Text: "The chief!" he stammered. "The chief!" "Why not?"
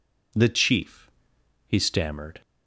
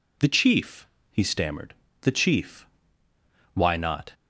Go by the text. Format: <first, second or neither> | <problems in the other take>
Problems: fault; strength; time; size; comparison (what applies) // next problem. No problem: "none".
second | stops before "The chief Why not"; at 2.4 s